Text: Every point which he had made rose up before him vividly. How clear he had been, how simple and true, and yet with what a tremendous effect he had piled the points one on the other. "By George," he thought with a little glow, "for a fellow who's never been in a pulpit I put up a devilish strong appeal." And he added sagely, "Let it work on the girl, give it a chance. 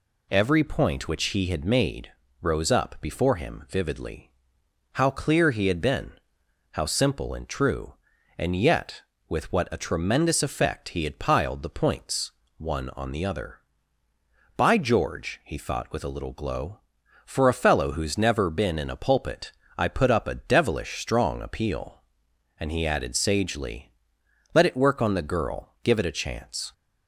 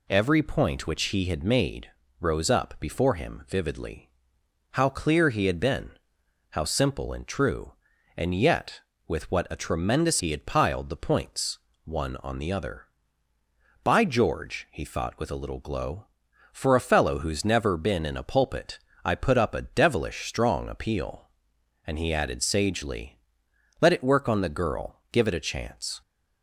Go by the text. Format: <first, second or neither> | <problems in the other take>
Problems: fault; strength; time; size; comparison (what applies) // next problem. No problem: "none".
first | pauses between "made" and "rose"; slight; at 1.8 s; 0.32 s long; slight in the first // skips "effect"; at 10.2 s // pauses between "points" and "one"; slight; at 11.5 s; 0.26 s long; slight in the first // pauses between "pulpit" and "I"; slight; at 18.7 s; 0.26 s long; slight in the first